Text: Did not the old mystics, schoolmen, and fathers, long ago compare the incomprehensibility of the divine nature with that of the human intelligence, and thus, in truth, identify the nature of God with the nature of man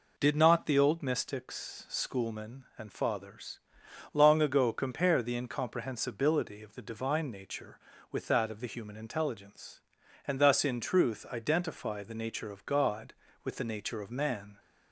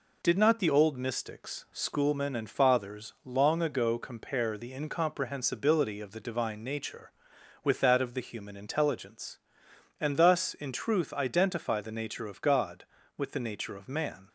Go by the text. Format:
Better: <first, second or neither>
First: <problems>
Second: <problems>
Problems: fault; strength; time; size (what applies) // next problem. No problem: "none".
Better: neither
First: none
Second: none